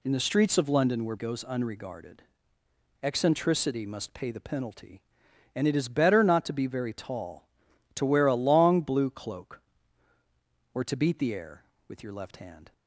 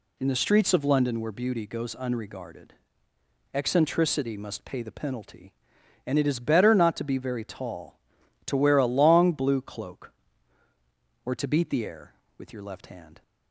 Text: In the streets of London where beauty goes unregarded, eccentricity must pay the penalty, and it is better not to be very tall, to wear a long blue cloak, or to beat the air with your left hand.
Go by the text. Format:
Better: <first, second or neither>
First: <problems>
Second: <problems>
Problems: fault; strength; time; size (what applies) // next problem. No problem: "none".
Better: second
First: skips "beauty"; at 1.1 s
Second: none